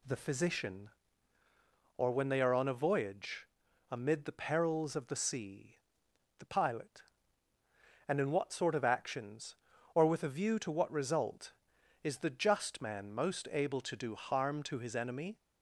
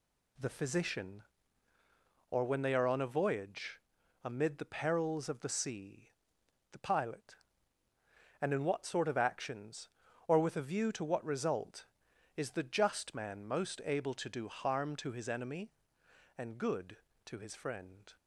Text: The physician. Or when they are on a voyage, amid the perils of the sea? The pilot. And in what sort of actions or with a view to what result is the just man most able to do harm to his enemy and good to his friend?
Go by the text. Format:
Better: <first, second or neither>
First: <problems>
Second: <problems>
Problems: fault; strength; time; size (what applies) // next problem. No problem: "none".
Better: second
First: stops before "and good to his friend"; at 15.3 s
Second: none